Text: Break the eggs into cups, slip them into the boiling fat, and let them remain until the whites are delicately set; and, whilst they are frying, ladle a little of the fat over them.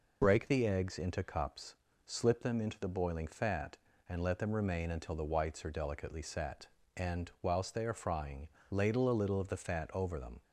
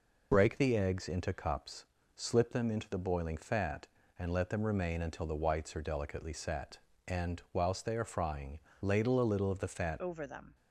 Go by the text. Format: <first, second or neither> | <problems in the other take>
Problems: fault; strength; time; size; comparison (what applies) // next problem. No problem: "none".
first | changes voice at "over"; from 9.9 s on; 0.6 s long